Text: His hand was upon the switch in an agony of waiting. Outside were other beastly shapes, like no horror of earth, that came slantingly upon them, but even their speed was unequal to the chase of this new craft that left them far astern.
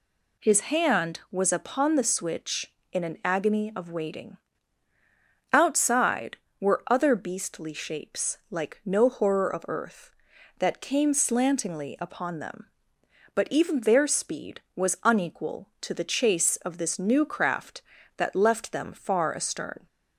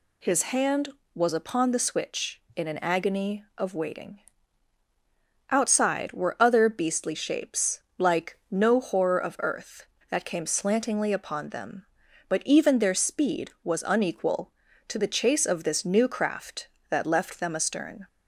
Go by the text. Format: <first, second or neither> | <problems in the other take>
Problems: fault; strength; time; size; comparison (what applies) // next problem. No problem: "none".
first | skips "far"; at 17.5 s